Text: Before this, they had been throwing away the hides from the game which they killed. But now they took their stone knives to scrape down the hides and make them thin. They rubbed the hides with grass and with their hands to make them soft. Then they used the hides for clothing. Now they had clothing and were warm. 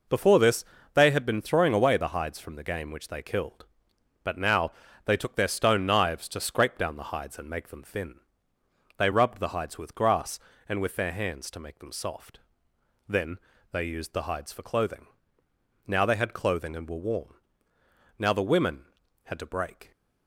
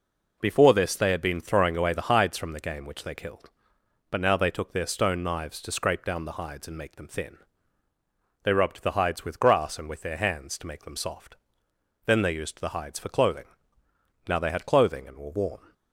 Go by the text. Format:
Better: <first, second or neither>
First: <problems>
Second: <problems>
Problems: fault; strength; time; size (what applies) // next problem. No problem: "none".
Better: second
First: pauses between "now" and "they"; slight; at 4.7 s; 0.32 s long // pauses between "Then" and "they"; slight; at 13.3 s; 0.34 s long // goes on to say "Now the women had to break"; strong; from 18.1 s on; 1.7 s long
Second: none